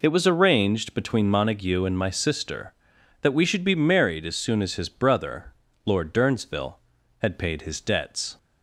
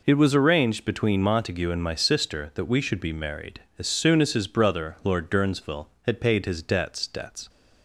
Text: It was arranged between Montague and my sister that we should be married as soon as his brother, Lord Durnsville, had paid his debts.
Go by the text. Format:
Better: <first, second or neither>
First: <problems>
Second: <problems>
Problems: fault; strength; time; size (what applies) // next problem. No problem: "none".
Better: first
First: none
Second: says "debts" twice; at 7.0 s